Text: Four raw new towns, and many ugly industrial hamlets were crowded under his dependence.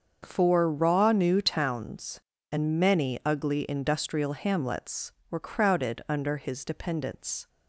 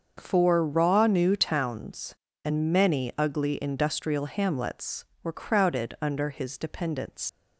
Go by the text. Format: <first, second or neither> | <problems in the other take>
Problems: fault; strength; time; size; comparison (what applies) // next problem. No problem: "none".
first | starts louder than the rest; until 1.1 s; 6.5 dB; also in the first // leaves "dependence" unfinished; at 7.2 s; 130 ms